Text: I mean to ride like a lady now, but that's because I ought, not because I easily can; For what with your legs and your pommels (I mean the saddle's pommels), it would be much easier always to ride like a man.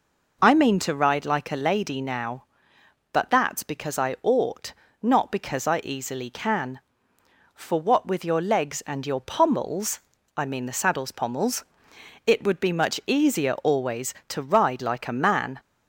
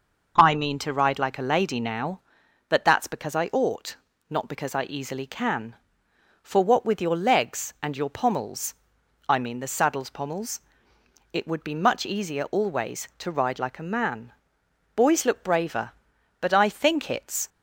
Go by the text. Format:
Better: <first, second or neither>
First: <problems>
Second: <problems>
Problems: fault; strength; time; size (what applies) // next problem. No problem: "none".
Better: first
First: none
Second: starts louder than the rest; until 1.3 s; 6.5 dB // goes on to say "Boys look braver but I think it's"; strong; from 14.9 s on; 2.5 s long